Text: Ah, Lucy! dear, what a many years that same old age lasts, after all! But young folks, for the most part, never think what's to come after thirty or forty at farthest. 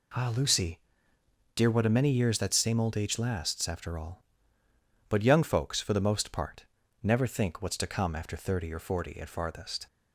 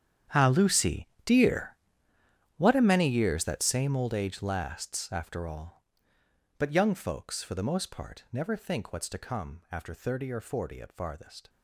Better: first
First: none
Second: gets quieter; strong; throughout; 17 dB

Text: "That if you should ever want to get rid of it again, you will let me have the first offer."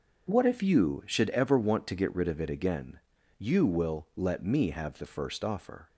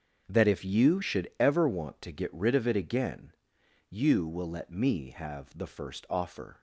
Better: second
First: starts louder than the rest; noticeable; until 1.3 s; 6 dB // says "What" for "That"; at 0.3 s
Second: starts louder than the rest; until 1.2 s; 6.5 dB

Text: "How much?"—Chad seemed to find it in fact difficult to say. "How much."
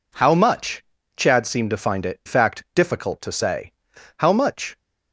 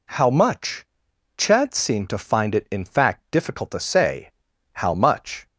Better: second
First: skips "in"; at 2.2 s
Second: none

